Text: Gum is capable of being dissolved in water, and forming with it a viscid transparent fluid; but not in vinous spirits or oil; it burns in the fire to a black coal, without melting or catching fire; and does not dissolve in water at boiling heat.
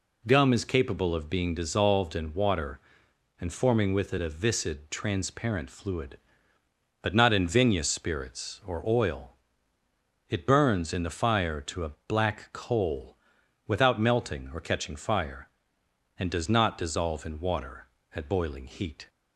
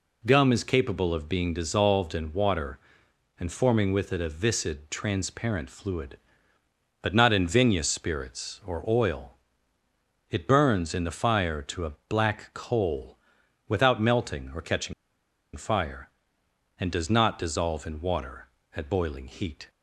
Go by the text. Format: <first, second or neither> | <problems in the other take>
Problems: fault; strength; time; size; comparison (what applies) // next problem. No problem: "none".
first | pauses between "catching" and "fire"; noticeable; at 14.9 s; 0.62 s long